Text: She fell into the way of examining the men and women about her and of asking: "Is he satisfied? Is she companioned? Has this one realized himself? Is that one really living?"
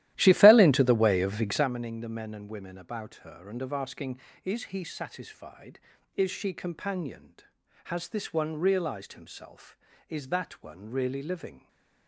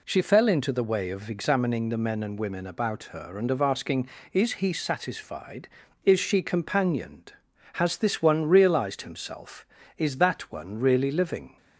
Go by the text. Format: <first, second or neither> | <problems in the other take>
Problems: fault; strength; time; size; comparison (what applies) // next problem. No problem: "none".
second | starts louder than the rest; strong; until 1.7 s; 14 dB